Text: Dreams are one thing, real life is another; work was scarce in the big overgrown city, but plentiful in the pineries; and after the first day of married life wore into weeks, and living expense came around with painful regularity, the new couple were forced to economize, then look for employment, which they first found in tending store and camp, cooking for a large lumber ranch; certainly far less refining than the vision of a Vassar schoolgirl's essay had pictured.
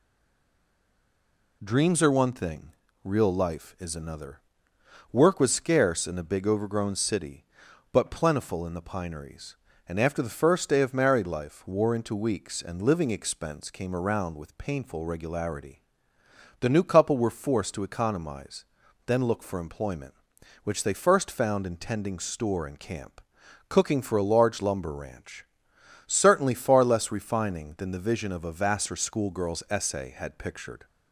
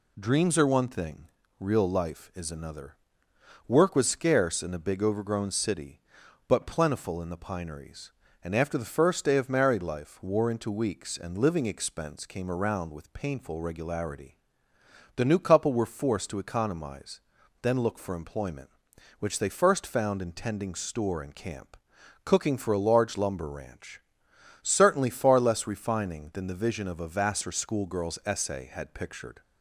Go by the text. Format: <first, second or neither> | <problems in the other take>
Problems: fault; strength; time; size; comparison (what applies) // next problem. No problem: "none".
second | stays silent before the first word; noticeable; until 1.6 s; 1.6 s long